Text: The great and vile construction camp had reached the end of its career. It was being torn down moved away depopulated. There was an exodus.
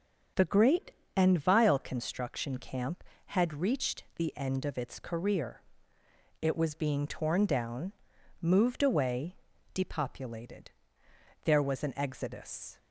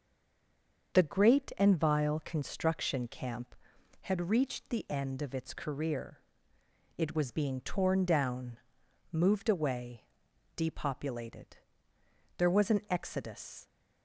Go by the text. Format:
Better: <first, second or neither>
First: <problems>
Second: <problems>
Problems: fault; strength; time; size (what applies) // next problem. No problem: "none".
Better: first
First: starts louder than the rest; until 1.6 s; 6.5 dB // pauses between "down" and "moved"; noticeable; at 7.9 s; 0.50 s long // pauses between "away" and "depopulated"; at 9.3 s; 0.38 s long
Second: stays silent before the first word; slight; until 0.9 s; 0.9 s long // starts louder than the rest; until 1.9 s; 6.5 dB // pauses between "down" and "moved"; noticeable; at 8.5 s; 0.52 s long // pauses between "away" and "depopulated"; noticeable; at 10.0 s; 0.52 s long